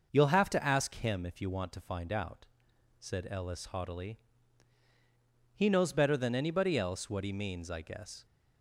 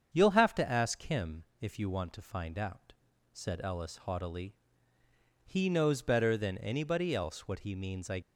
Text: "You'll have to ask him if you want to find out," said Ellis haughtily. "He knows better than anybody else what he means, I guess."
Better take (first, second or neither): first